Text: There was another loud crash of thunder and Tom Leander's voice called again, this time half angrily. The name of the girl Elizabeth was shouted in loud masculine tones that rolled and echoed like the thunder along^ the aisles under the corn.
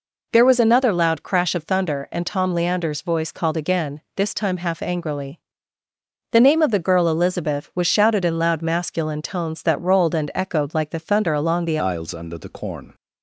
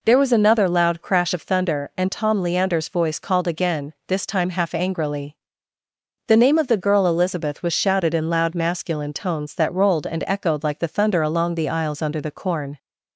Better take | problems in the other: second | changes voice at "aisles"; from 11.7 s on; 1.2 s long

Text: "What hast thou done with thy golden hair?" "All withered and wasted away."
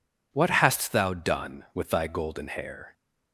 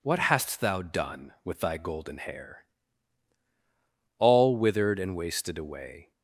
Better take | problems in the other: second | stops before "All withered and wasted away"; at 2.9 s

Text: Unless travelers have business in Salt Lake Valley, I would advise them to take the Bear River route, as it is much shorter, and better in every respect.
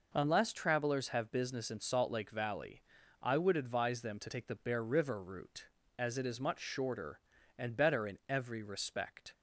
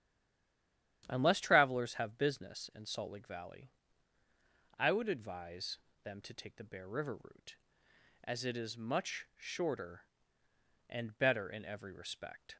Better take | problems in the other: first | stays silent before the first word; until 1.0 s; 1.0 s long // starts louder than the rest; strong; until 2.0 s; 10.5 dB // pauses between "advise" and "them"; slight; at 5.7 s; 0.24 s long

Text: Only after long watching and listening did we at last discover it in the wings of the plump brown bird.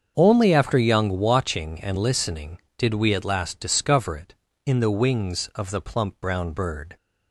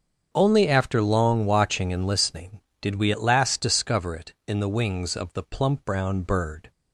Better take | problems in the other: second | starts louder than the rest; until 1.1 s; 7 dB; also in the second // says "young" for "long"; at 0.7 s

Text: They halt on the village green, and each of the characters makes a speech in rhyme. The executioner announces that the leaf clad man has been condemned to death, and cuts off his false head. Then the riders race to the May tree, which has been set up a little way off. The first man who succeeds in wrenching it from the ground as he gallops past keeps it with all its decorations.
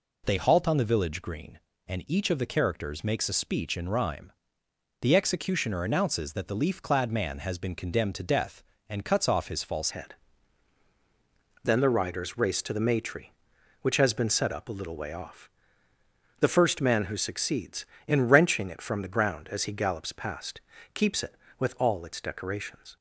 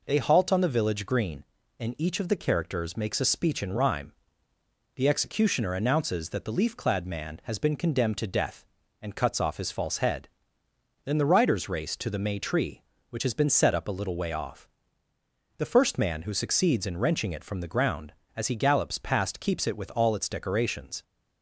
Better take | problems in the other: second | changes voice at "head"; from 9.8 s on; 13.1 s long // pauses between "past" and "keeps"; slight; at 20.6 s; 0.32 s long

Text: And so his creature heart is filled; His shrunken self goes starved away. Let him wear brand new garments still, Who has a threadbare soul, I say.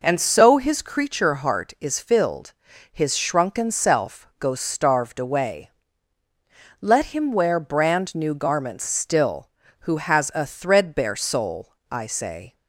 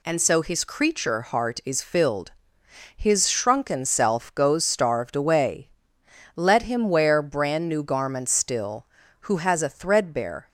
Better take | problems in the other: first | stops before "soul I say"; at 10.4 s

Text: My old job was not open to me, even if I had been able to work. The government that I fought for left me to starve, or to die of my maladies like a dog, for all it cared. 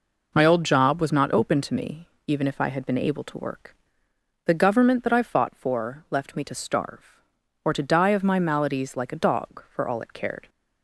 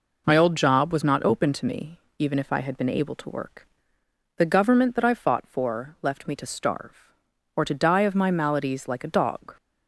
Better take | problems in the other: first | stops before "for all it cared"; at 9.5 s

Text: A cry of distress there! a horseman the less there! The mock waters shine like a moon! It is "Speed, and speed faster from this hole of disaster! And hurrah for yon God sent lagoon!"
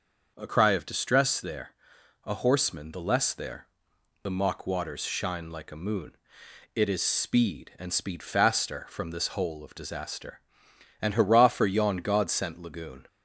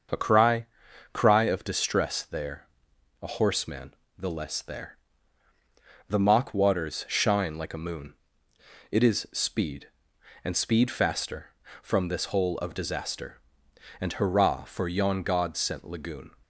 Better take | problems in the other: first | starts louder than the rest; until 1.6 s; 6.5 dB; also in the first // says "cry" twice; at 1.1 s // pauses between "horseman" and "the"; slight; at 3.9 s; 0.24 s long

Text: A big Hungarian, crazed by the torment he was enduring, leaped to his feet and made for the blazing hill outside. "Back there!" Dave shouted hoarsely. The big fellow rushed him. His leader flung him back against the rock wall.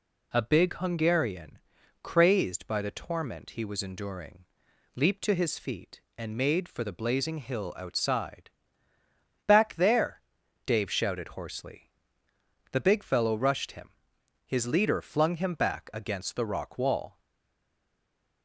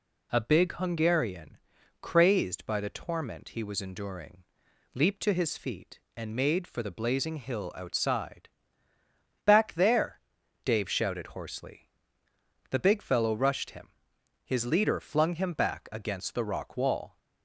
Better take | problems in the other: second | stays silent after the last word; noticeable; from 17.1 s on; 1.3 s long

